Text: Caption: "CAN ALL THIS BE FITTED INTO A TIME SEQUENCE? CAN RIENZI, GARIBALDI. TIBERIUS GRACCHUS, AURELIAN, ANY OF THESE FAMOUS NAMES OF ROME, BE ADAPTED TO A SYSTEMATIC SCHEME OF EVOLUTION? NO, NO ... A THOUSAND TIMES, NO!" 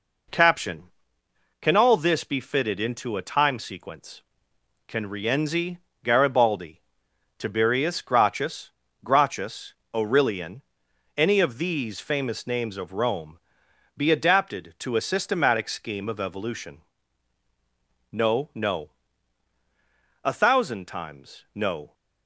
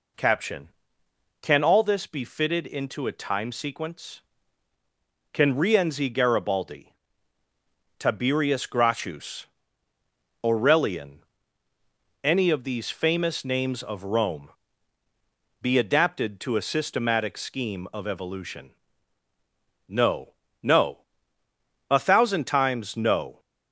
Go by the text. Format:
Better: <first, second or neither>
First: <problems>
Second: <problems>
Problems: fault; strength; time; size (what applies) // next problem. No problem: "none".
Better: second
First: says "GRACCHUS" twice; at 9.0 s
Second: none